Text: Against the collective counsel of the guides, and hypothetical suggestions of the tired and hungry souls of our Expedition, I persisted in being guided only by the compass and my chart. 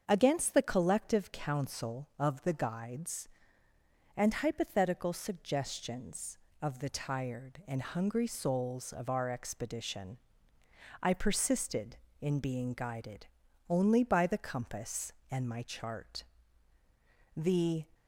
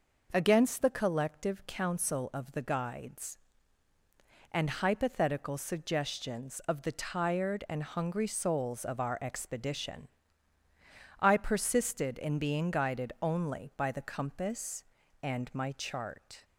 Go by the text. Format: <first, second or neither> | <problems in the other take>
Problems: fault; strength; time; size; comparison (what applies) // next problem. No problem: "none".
second | starts louder than the rest; until 1.0 s; 7 dB // pauses between "guided" and "only"; at 13.2 s; 0.42 s long // goes on to say "The"; from 17.3 s on; 0.50 s long